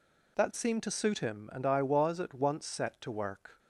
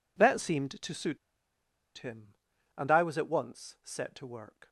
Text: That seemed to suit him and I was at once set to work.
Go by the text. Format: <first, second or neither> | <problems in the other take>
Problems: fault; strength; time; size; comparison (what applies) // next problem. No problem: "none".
first | pauses between "suit" and "him"; noticeable; at 1.1 s; 0.80 s long